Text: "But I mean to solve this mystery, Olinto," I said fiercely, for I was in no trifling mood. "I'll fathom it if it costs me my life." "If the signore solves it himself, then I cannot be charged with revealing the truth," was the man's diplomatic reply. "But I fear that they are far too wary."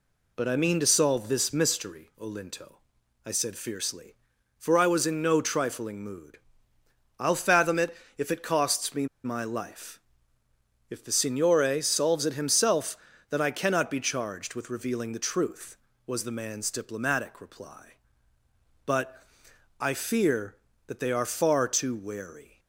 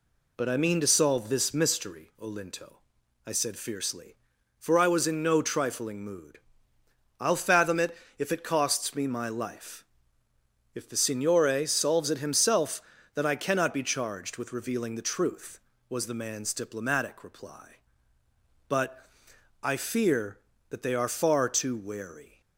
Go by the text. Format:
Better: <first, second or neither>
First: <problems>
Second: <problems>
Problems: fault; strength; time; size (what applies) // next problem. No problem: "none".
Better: second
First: pauses between "it" and "if"; slight; at 7.9 s; 0.22 s long // pauses between "me" and "my"; slight; at 9.0 s; 0.18 s long // pauses between "But" and "I"; noticeable; at 19.2 s; 0.56 s long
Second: pauses between "it" and "if"; slight; at 7.9 s; 0.22 s long // pauses between "But" and "I"; noticeable; at 19.0 s; 0.56 s long